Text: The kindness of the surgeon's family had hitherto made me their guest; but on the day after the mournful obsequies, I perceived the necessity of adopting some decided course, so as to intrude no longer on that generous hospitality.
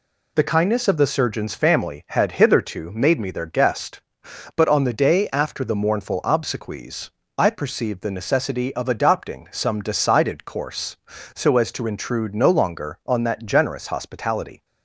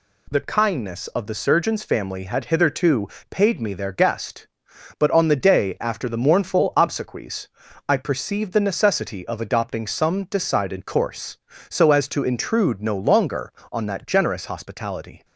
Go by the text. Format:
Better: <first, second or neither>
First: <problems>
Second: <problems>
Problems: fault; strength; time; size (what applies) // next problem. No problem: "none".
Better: first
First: none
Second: says "paid" for "made"; at 3.3 s